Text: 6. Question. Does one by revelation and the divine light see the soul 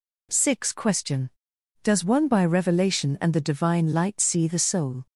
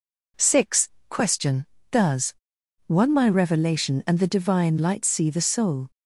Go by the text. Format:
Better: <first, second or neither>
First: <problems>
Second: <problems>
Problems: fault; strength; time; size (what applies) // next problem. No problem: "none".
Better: first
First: none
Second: pauses between "Does" and "one"; noticeable; at 2.3 s; 0.54 s long // says "my" for "by"; at 3.1 s